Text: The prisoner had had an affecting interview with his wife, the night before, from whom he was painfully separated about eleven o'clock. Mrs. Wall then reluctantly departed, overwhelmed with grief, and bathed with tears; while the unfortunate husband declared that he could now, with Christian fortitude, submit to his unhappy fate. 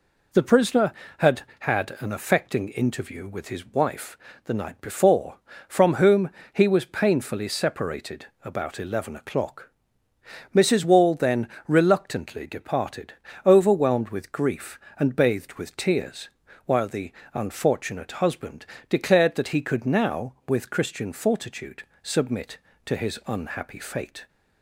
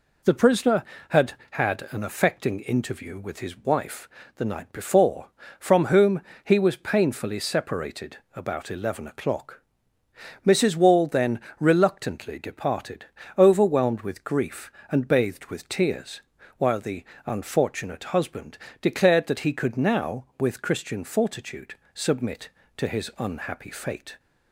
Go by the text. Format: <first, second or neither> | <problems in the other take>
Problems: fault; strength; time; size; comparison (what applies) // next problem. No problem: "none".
neither | pauses between "whom" and "he"; slight; the same in both // pauses between "separated" and "about"; slight; the same in both // pauses between "then" and "reluctantly"; slight; the same in both // pauses between "the" and "unfortunate"; slight; the same in both // pauses between "husband" and "declared"; slight; the same in both